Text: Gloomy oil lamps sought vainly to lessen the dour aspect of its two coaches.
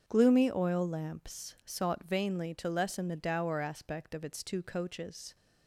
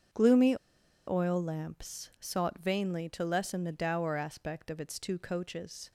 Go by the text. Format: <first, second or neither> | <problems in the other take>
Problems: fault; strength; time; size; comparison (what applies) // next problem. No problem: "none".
first | starts louder than the rest; until 1.6 s; 7 dB; also in the first // pauses between "Gloomy" and "oil"; noticeable; at 0.5 s; 0.51 s long